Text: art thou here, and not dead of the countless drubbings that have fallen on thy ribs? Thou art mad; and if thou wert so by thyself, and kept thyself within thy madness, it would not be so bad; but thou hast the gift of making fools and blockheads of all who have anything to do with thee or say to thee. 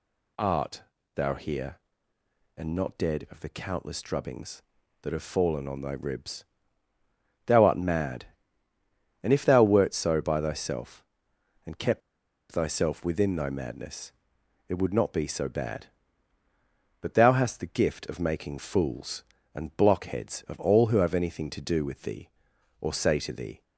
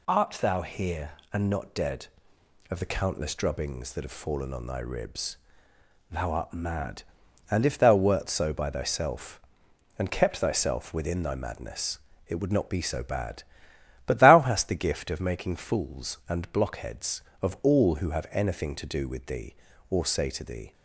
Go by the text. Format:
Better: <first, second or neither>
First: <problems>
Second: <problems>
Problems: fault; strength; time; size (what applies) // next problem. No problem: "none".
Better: second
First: pauses between "art" and "thou"; slight; at 0.8 s; 0.34 s long // pauses between "kept" and "thyself"; noticeable; at 12.0 s; 0.51 s long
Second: none